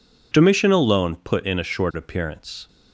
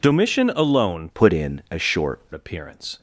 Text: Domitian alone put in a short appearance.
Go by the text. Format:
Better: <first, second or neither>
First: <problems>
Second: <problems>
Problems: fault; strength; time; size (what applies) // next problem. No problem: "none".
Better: first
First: none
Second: changes voice from "put" to "short"; from 1.1 to 2.2 s; 1.1 s long